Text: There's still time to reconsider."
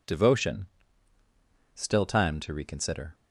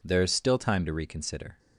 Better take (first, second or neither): second